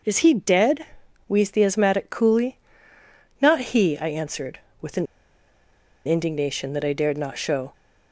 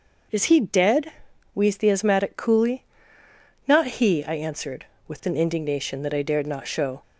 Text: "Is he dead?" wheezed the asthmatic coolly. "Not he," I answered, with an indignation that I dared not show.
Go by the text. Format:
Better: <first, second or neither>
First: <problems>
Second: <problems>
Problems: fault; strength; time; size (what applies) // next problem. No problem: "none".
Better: second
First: pauses between "an" and "indignation"; at 5.0 s; 1.0 s long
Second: none